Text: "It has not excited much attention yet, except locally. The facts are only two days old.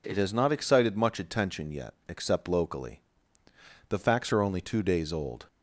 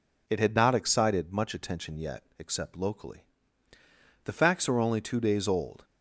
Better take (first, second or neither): first